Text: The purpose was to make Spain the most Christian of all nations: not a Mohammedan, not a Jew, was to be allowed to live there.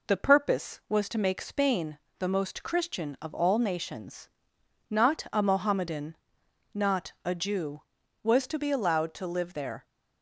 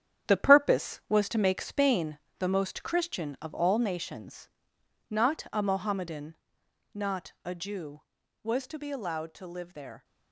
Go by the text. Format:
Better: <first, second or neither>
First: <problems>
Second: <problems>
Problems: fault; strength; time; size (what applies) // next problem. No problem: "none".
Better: first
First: pauses between "Spain" and "the"; slight; at 1.9 s; 0.22 s long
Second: gets quieter; strong; throughout; 8.5 dB // pauses between "Spain" and "the"; slight; at 2.1 s; 0.22 s long